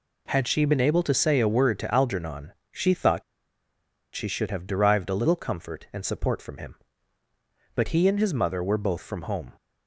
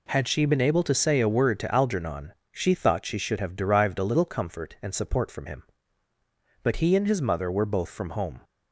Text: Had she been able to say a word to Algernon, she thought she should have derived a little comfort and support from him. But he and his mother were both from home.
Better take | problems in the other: second | pauses between "thought" and "she"; noticeable; at 3.2 s; 0.92 s long

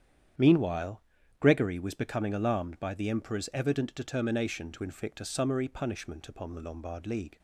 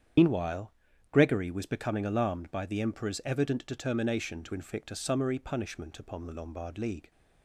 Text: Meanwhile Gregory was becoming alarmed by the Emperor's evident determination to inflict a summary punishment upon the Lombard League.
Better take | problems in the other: first | loses the start of "Meanwhile"; at 0.1 s; 90 ms // starts louder than the rest; strong; until 1.5 s; 8.5 dB; strong in the first // pauses between "Meanwhile" and "Gregory"; at 0.7 s; 0.38 s long; also in the first

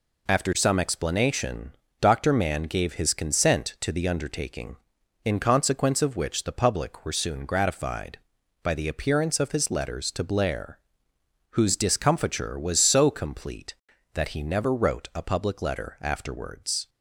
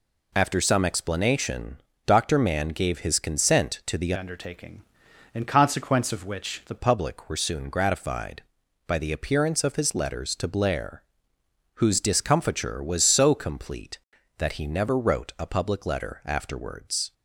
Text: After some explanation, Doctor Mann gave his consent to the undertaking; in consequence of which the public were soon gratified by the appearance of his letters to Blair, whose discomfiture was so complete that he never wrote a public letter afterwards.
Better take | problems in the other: first | changes voice from "undertaking" to "the"; from 4.1 to 6.7 s; 2.6 s long

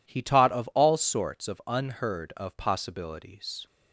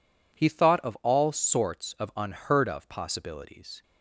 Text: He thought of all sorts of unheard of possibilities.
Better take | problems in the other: second | says "taught" for "thought"; at 0.2 s

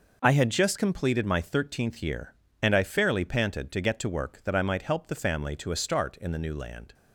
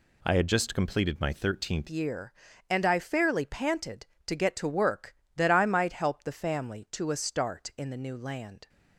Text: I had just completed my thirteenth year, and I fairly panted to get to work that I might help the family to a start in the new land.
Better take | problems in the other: first | changes voice at "year"; from 1.9 s on; 6.7 s long

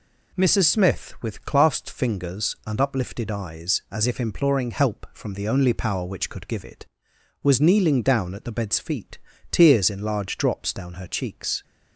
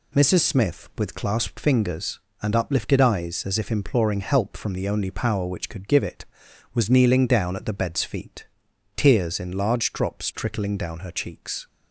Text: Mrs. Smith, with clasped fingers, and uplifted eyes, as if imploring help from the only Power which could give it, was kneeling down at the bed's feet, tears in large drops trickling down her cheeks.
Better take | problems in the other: second | skips "trickling"; at 10.7 s

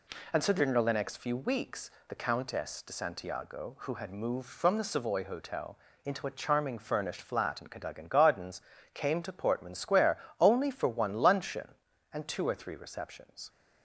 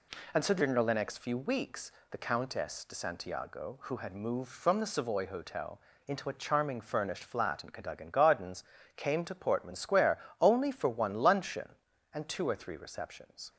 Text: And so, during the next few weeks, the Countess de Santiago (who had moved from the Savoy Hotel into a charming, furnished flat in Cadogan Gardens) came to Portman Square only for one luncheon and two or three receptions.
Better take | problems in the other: neither | pauses between "Hotel" and "into"; slight; the same in both // pauses between "Square" and "only"; slight; the same in both

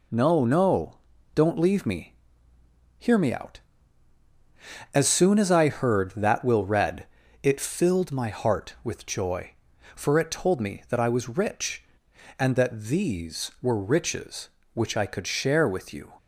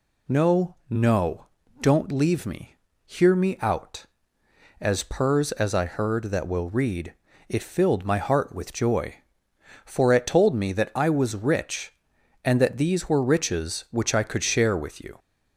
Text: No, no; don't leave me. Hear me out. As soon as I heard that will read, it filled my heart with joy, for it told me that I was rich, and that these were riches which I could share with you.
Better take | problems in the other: first | says "purrs" for "soon"; at 5.0 s

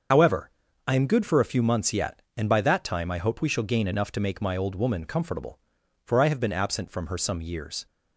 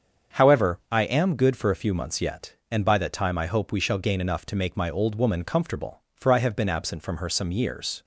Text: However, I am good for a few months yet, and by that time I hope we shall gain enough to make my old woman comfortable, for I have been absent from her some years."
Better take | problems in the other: second | loses the start of "However"; at 0.1 s; 45 ms // starts louder than the rest; until 1.4 s; 7 dB; strong in the second

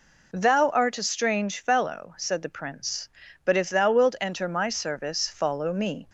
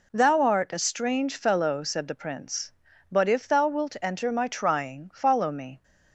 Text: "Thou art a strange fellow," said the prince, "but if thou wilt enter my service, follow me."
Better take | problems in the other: first | says "trying" for "service"; at 4.4 s

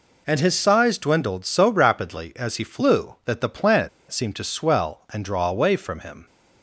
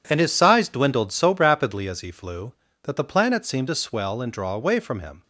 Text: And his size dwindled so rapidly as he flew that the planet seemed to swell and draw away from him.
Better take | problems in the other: second | pauses between "planet" and "seemed"; slight; at 3.8 s; 0.22 s long

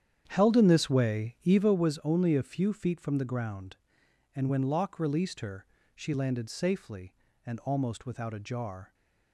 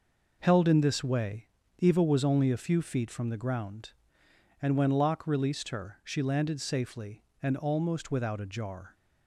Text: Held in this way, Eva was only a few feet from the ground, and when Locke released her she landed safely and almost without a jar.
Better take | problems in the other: second | starts louder than the rest; strong; until 1.8 s; 9 dB // pauses between "her" and "she"; slight; at 5.6 s; 0.28 s long

